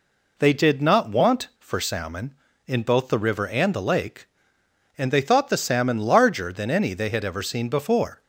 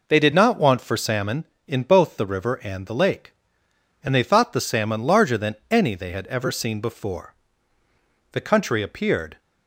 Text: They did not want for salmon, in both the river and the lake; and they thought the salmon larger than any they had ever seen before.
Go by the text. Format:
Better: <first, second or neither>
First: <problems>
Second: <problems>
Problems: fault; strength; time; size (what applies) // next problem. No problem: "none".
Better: first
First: none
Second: goes on to say "The country appeared"; noticeable; from 8.3 s on; 1.0 s long